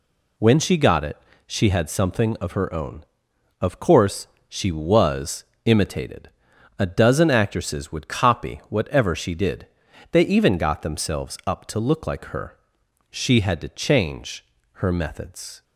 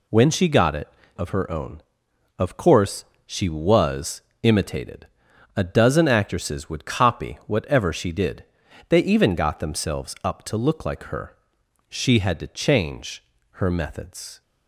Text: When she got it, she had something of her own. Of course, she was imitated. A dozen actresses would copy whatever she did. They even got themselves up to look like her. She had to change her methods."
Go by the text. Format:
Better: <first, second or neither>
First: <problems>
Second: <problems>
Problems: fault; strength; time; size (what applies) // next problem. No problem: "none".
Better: first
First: pauses between "was" and "imitated"; slight; at 5.4 s; 0.20 s long // pauses between "change" and "her"; slight; at 14.4 s; 0.34 s long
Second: skips "she had something"; at 1.0 s // pauses between "was" and "imitated"; slight; at 4.2 s; 0.20 s long // pauses between "change" and "her"; slight; at 13.2 s; 0.34 s long